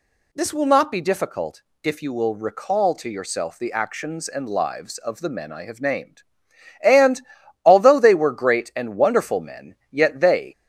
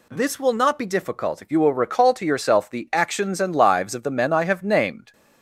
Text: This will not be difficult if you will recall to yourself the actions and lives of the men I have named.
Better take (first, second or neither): second